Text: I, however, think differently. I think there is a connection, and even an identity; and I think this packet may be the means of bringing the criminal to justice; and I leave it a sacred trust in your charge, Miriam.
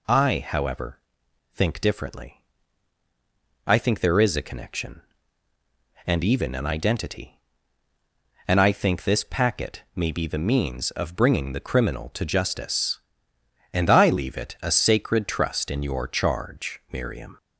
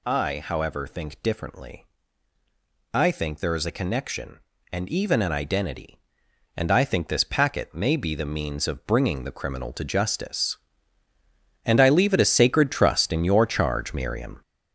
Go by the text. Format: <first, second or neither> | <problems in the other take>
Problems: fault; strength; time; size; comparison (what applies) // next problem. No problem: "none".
first | gets louder; strong; throughout; 7.5 dB